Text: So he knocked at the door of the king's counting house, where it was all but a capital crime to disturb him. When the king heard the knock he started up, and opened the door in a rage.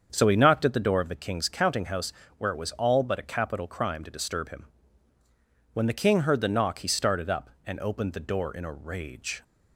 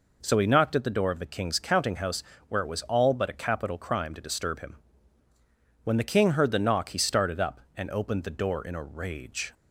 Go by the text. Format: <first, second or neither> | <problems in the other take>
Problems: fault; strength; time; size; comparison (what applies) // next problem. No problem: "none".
second | starts louder than the rest; until 1.3 s; 7 dB